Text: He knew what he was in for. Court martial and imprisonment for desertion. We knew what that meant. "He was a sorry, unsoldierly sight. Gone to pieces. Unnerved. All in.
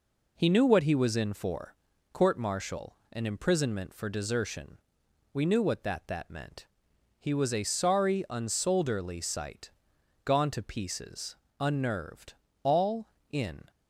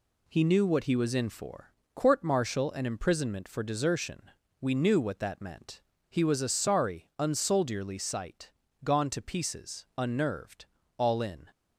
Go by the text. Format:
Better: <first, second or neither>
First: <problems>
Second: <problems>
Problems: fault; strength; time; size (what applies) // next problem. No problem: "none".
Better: second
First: says "that" twice; at 6.0 s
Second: none